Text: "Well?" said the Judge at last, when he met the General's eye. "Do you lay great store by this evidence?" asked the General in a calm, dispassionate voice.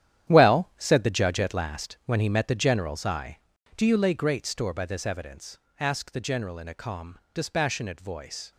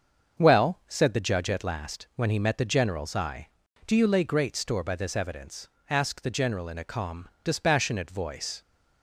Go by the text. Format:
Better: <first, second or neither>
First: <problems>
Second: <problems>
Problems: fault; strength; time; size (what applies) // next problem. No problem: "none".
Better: second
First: gets quieter; strong; throughout; 12 dB // starts louder than the rest; strong; until 1.3 s; 11 dB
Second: starts louder than the rest; until 1.4 s; 6.5 dB